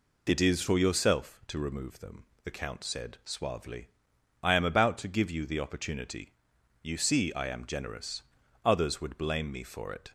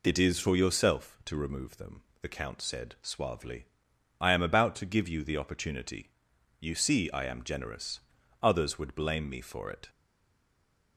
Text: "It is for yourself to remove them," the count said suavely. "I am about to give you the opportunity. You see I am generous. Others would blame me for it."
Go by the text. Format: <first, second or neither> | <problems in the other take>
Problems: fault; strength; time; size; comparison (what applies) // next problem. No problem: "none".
first | stays silent after the last word; from 9.8 s on; 1.1 s long